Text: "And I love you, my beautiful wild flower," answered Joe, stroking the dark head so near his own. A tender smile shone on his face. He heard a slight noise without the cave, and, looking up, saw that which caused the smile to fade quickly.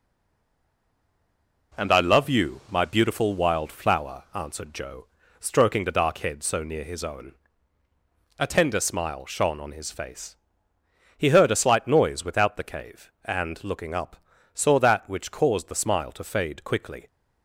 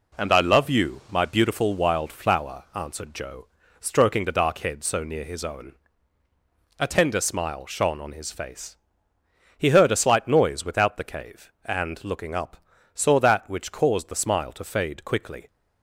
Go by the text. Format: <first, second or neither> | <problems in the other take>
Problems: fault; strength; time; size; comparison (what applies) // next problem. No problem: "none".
second | stays silent before the first word; noticeable; until 1.7 s; 1.7 s long